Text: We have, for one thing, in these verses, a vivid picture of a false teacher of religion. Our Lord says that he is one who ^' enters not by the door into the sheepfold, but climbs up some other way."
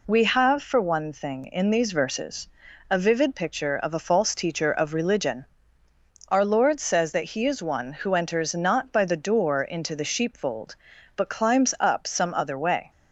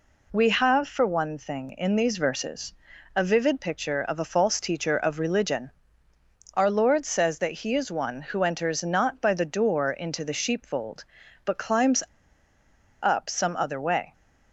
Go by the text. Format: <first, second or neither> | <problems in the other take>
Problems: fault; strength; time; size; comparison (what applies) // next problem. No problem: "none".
first | pauses between "climbs" and "up"; at 12.0 s; 1.0 s long